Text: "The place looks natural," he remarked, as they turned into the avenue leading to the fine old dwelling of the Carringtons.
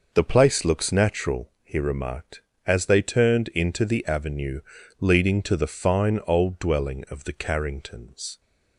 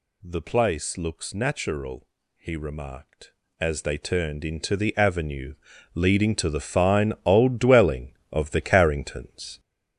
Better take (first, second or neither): first